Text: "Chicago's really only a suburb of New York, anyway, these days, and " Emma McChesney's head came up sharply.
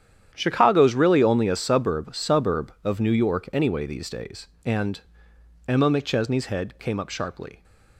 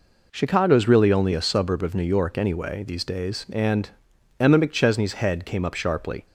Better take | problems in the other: second | starts louder than the rest; strong; until 1.3 s; 10 dB // says "suburb" twice; at 2.1 s

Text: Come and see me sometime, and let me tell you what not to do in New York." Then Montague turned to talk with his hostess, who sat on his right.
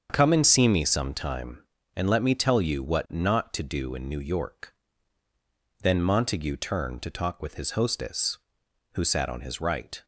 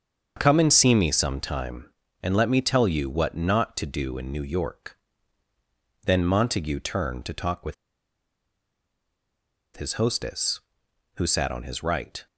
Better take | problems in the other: first | starts louder than the rest; until 1.4 s; 7 dB; also in the first // pauses between "with" and "his"; strong; at 7.7 s; 2.0 s long

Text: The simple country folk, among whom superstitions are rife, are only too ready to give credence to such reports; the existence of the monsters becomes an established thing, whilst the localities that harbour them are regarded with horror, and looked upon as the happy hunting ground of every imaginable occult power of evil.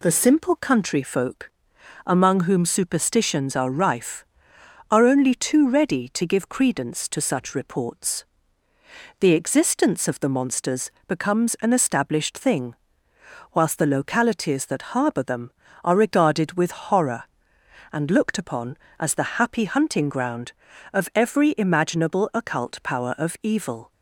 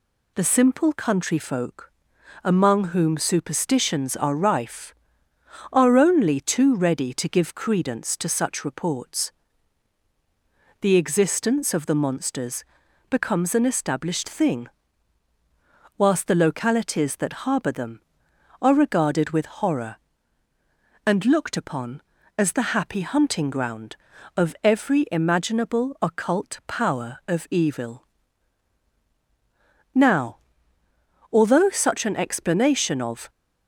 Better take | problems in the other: first | pauses between "monsters" and "becomes"; noticeable; at 12.6 s; 0.48 s long; slight in the first // pauses between "with" and "horror"; slight; at 19.4 s; 0.16 s long // goes on to say "Now although such an explanation of"; strong; from 29.9 s on; 3.3 s long

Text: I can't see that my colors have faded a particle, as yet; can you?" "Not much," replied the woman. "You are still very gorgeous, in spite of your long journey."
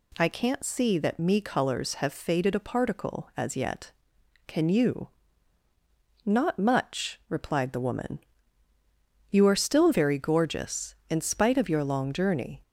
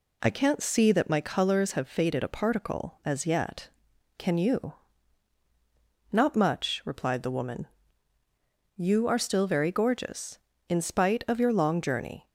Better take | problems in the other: second | says "me" for "my"; at 1.1 s

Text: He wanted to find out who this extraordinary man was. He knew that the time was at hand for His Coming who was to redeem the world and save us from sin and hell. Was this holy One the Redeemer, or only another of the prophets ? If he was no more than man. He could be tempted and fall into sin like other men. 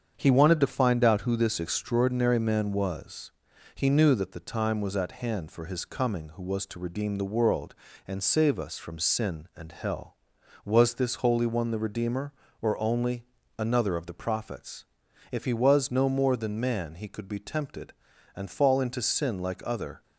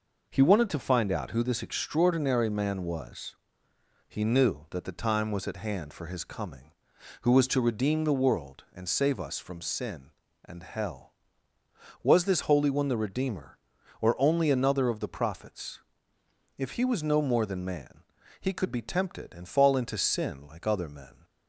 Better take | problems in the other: second | starts louder than the rest; strong; until 1.1 s; 7.5 dB // pauses between "only" and "another"; slight; at 13.2 s; 0.32 s long // stops before "men"; at 20.0 s

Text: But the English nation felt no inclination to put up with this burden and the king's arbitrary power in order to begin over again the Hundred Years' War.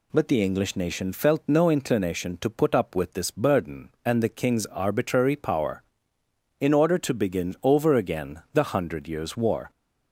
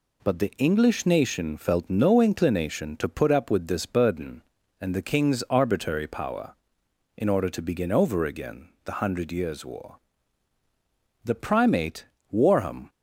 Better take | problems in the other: first | pauses between "again" and "the"; slight; at 8.6 s; 0.16 s long // goes on to say "The primate Warham"; from 11.2 s on; 1.6 s long

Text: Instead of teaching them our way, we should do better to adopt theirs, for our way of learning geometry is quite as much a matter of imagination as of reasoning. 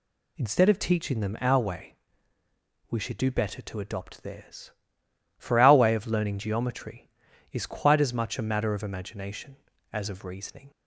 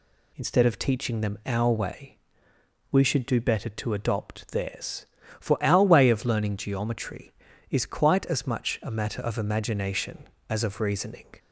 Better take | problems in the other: neither | none

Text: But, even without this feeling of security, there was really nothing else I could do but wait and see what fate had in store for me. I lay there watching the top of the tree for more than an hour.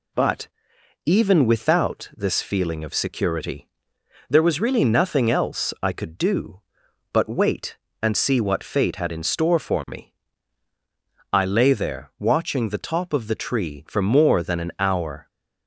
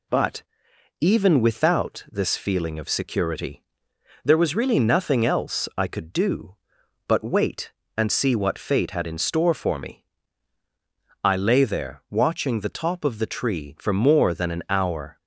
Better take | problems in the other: neither | none

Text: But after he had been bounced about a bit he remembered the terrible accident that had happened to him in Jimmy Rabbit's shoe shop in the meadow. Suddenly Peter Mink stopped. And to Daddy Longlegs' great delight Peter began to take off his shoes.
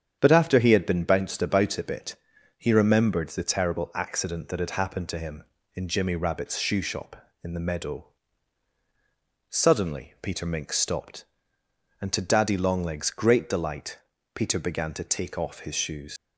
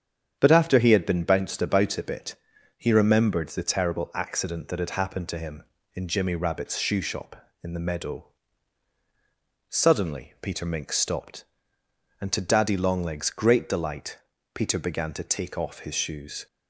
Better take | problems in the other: second | starts louder than the rest; strong; until 1.2 s; 8.5 dB; strong in the second // pauses between "bit" and "he"; at 2.1 s; 0.44 s long; also in the second // pauses between "delight" and "Peter"; slight; at 13.9 s; 0.34 s long; slight in the second // leaves "shoes" unfinished; at 16.1 s; 105 ms

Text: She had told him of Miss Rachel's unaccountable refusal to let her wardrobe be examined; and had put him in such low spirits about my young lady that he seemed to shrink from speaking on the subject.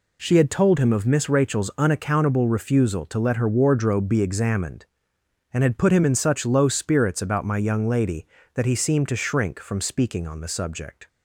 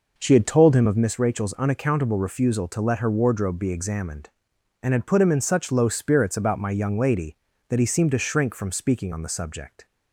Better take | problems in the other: first | starts louder than the rest; noticeable; until 1.1 s; 5 dB

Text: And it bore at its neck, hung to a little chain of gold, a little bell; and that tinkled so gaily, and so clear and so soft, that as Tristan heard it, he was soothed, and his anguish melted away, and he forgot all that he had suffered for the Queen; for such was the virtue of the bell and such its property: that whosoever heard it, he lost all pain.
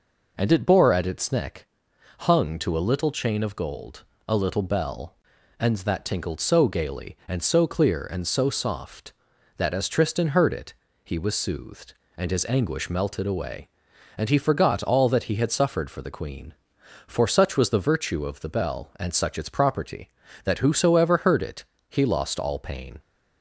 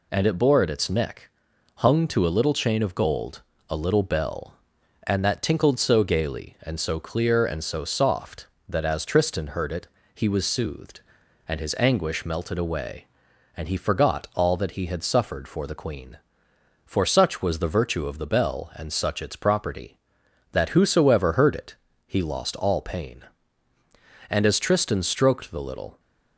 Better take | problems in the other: first | goes on to say "And as Tristan stroked the little"; strong; from 24.2 s on; 1.7 s long

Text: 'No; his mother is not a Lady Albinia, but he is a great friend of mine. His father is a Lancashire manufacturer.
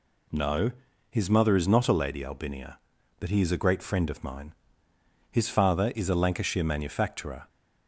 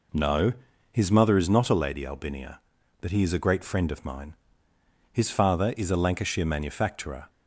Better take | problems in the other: first | starts louder than the rest; noticeable; until 1.5 s; 4 dB

